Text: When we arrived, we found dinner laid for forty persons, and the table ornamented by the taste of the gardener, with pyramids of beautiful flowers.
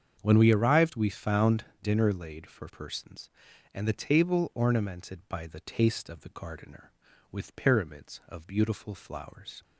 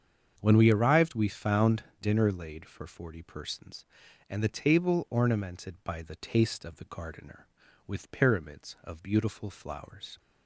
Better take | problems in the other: second | starts louder than the rest; strong; until 1.2 s; 7.5 dB; strong in the second // pauses between "found" and "dinner"; slight; at 1.6 s; 0.18 s long; slight in the second // skips "forty"; at 2.6 s

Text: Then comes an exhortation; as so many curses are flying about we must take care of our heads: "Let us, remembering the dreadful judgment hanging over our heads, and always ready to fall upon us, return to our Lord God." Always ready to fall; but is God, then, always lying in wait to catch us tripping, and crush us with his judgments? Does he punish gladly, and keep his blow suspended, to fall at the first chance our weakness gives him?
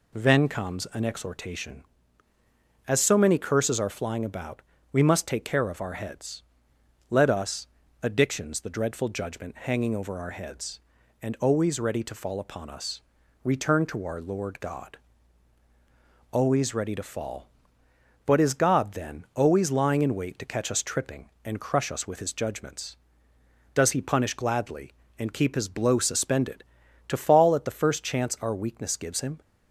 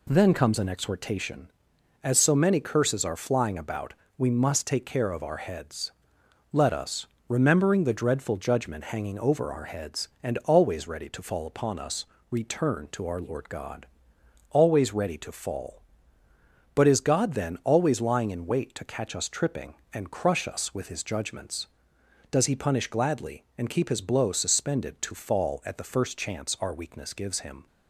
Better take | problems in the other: second | pauses between "about" and "we"; slight; at 4.6 s; 0.32 s long; slight in the second // says "addictions" for "remembering"; at 8.0 s

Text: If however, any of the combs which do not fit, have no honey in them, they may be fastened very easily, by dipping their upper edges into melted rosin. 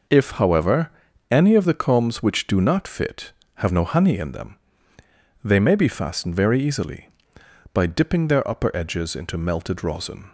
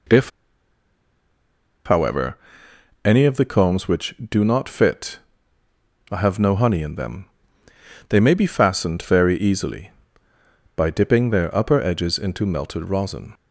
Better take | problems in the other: first | pauses between "If" and "however"; strong; at 0.2 s; 1.5 s long

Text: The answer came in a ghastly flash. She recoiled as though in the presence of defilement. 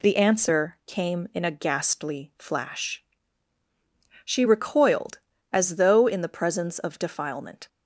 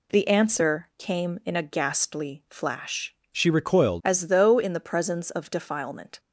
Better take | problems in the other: first | changes voice from "She" to "recoiled"; from 3.3 to 4.0 s; 0.7 s long

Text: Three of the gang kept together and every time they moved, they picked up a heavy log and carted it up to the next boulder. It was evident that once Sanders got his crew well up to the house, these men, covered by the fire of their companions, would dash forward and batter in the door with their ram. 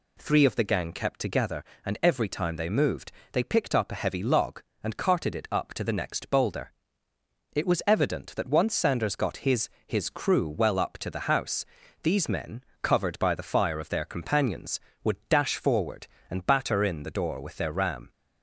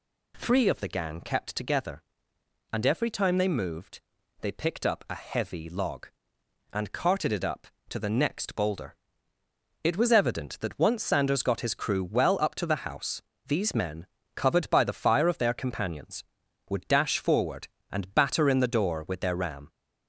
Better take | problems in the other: second | says "his" twice; at 9.8 s

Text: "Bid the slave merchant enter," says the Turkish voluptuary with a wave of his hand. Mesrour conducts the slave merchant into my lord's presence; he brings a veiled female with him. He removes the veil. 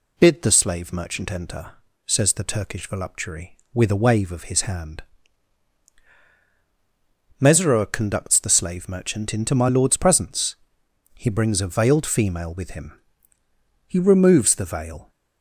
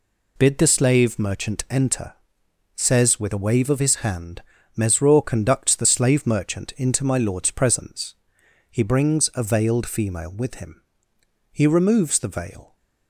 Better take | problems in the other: first | skips "the Turkish voluptuary"; at 3.1 s

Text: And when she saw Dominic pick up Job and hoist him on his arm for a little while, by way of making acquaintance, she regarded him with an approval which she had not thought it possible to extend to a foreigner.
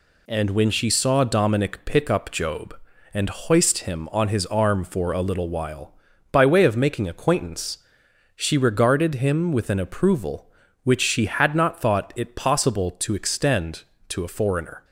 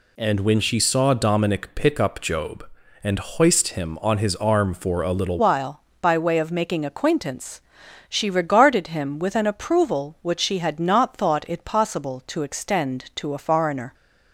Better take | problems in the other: first | changes voice at "while"; from 5.3 s on; 8.6 s long

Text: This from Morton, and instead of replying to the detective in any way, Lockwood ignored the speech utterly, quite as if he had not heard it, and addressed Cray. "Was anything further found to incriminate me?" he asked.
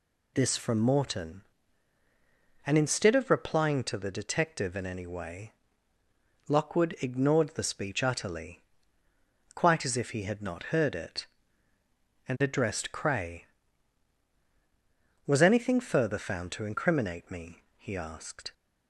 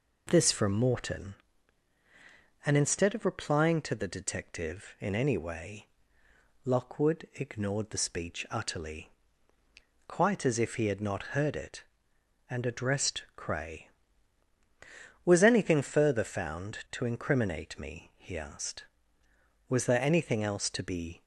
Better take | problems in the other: first | goes on to say "Was there anything else to be"; from 19.6 s on; 1.5 s long

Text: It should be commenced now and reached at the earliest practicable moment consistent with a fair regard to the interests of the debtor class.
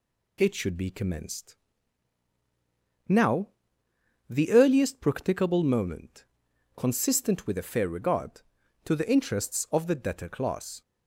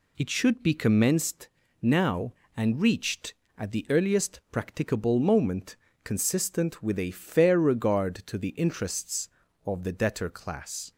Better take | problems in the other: second | pauses between "commenced" and "now"; strong; at 1.5 s; 1.5 s long; slight in the second // skips "and reached at"; at 3.8 s // pauses between "moment" and "consistent"; noticeable; at 6.2 s; 0.54 s long; slight in the second

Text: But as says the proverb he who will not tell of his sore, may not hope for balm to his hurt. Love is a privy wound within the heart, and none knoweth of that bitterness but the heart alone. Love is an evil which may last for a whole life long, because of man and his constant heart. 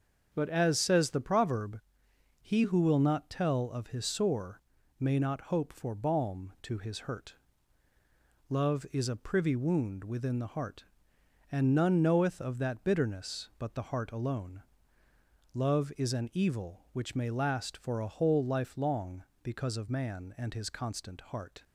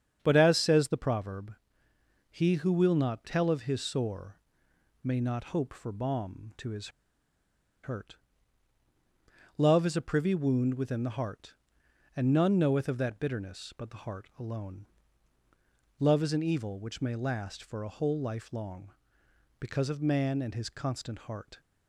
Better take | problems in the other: first | starts louder than the rest; strong; until 1.2 s; 8 dB; also in the first // pauses between "proverb" and "he"; noticeable; at 1.5 s; 0.78 s long; noticeable in the first // pauses between "his" and "hurt"; noticeable; at 6.8 s; 0.93 s long

